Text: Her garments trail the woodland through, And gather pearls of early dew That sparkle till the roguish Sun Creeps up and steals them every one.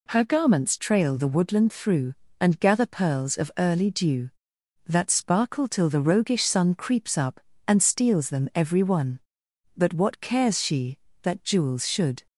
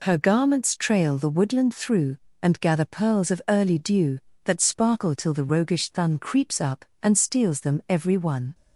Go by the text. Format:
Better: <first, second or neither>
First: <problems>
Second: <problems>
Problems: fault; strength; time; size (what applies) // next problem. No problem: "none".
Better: second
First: goes on to say "But what cares she that jewels should"; strong; from 9.7 s on; 2.5 s long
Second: none